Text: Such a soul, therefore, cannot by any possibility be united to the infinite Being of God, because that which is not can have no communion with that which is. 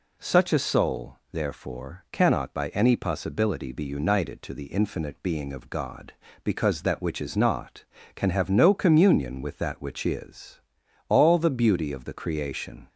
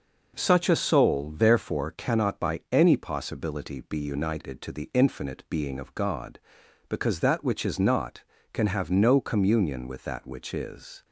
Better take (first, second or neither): second